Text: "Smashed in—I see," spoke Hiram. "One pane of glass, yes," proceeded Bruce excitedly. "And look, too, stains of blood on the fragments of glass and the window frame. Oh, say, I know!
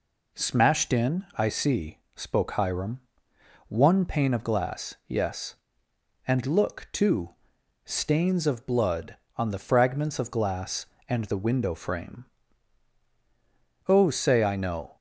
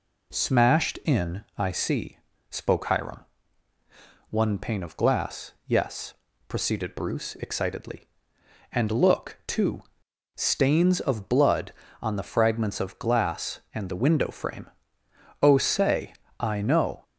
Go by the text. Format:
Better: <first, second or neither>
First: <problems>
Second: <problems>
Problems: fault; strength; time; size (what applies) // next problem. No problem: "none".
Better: second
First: skips "proceeded Bruce excitedly"; at 5.9 s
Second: none